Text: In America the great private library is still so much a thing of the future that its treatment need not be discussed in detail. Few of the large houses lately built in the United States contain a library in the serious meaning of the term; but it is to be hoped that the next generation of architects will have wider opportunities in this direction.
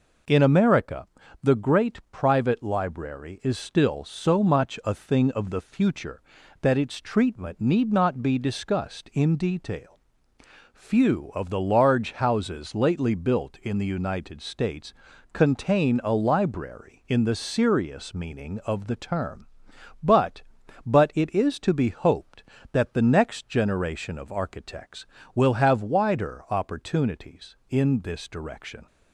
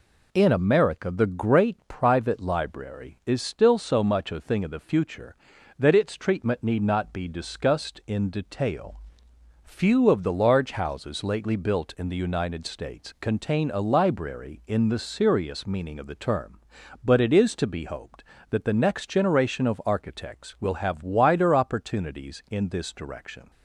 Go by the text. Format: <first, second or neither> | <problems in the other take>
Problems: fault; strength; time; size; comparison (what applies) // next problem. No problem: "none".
second | pauses between "America" and "the"; slight; at 1.0 s; 0.34 s long // pauses between "States" and "contain"; at 14.9 s; 0.38 s long // says "but" twice; at 20.8 s